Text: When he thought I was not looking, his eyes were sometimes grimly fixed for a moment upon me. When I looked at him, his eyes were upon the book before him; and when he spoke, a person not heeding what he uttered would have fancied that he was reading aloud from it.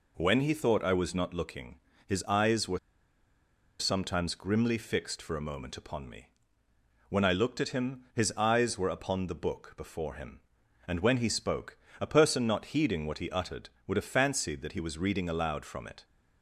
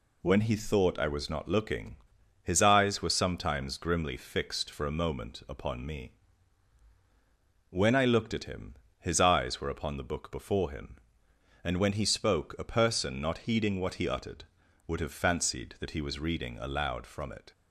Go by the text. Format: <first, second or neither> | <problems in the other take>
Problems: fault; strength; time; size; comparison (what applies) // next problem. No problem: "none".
second | pauses between "were" and "sometimes"; at 2.7 s; 1.0 s long